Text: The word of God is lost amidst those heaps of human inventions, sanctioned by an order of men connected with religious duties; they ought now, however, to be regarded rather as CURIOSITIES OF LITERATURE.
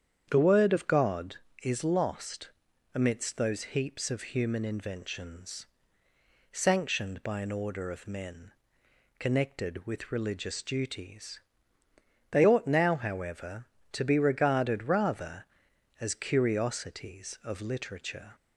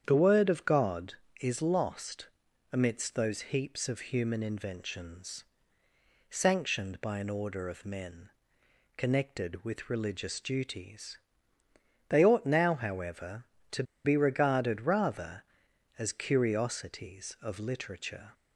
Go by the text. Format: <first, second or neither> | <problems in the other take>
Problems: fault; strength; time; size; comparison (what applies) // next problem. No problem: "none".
first | starts louder than the rest; strong; until 1.0 s; 8.5 dB; strong in the first // pauses between "lost" and "amidst"; at 2.2 s; 0.44 s long; also in the first // pauses between "men" and "connected"; noticeable; at 8.2 s; 0.68 s long; noticeable in the first // pauses between "to" and "be"; slight; at 13.8 s; 0.21 s long